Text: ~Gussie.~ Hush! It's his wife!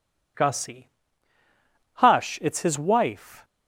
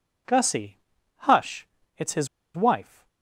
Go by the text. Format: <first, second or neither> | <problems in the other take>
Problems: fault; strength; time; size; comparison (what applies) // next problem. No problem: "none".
first | pauses between "his" and "wife"; slight; at 2.2 s; 0.27 s long